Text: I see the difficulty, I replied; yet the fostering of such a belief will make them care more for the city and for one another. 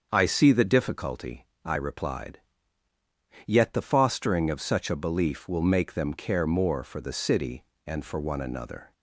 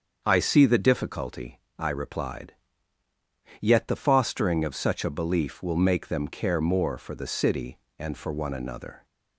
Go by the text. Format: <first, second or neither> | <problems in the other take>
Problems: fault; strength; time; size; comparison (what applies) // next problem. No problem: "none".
neither | starts louder than the rest; the same in both